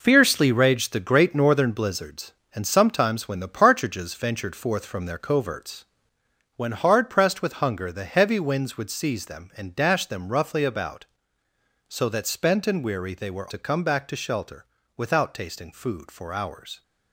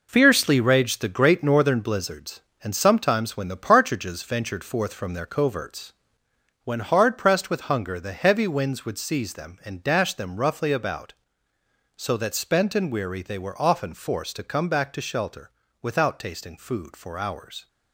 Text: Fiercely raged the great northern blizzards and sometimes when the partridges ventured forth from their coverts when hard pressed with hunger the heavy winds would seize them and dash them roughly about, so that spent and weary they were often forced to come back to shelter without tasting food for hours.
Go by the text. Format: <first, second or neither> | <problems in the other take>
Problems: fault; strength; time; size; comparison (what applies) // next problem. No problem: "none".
second | pauses between "coverts" and "when"; noticeable; at 5.8 s; 0.70 s long; noticeable in the second // skips "often forced"; at 13.5 s // pauses between "shelter" and "without"; slight; at 14.6 s; 0.32 s long; slight in the second